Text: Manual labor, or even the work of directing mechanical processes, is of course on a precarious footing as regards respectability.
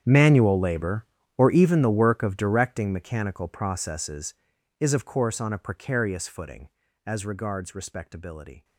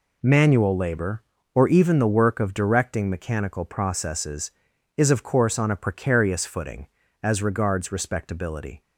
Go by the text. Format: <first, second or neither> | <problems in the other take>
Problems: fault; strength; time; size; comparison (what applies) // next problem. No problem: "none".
second | gets quieter; strong; throughout; 19.5 dB